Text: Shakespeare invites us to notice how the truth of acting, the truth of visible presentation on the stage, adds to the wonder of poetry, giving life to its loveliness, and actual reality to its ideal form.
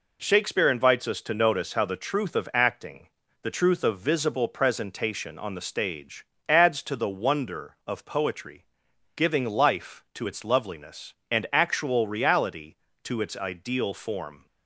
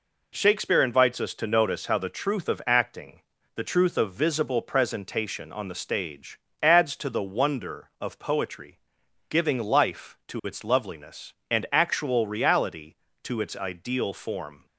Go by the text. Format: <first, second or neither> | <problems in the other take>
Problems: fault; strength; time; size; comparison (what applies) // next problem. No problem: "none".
neither | none